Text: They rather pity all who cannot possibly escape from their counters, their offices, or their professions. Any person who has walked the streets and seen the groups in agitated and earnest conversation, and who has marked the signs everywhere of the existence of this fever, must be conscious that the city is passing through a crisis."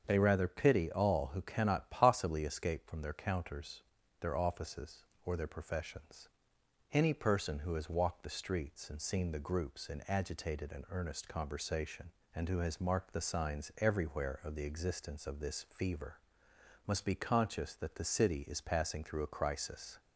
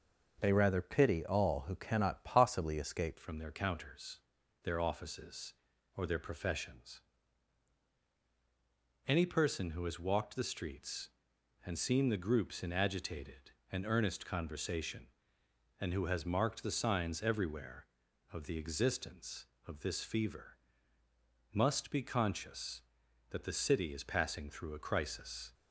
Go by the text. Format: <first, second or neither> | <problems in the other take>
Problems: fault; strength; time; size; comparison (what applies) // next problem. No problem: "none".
first | starts louder than the rest; noticeable; until 1.4 s; 6 dB; also in the first // changes voice at "from"; from 3.1 s on; 22.4 s long